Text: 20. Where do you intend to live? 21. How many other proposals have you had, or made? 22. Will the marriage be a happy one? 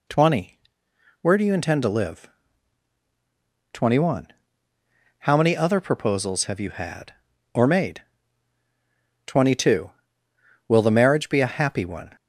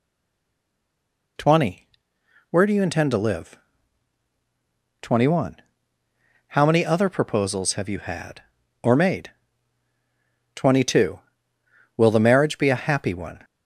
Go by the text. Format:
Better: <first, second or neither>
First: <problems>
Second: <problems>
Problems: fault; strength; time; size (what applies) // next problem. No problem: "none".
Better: first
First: none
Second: stays silent before the first word; noticeable; until 1.3 s; 1.3 s long